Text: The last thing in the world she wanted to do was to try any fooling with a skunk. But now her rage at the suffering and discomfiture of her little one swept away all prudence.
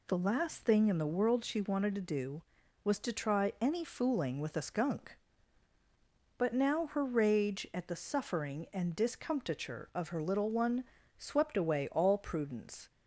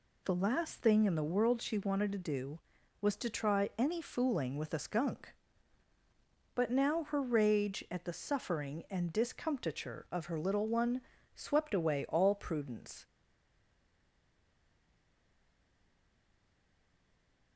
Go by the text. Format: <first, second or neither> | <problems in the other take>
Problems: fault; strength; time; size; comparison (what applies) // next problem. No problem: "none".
first | pauses between "one" and "swept"; slight; at 11.0 s; 0.34 s long; slight in the first // stays silent after the last word; strong; from 13.0 s on; 4.5 s long